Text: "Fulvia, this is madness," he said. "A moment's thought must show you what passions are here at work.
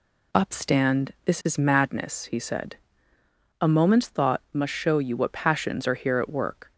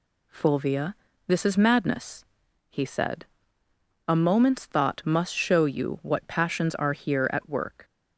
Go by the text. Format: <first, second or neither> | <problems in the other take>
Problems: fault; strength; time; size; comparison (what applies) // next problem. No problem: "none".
second | says "Upstand" for "Fulvia"; at 0.3 s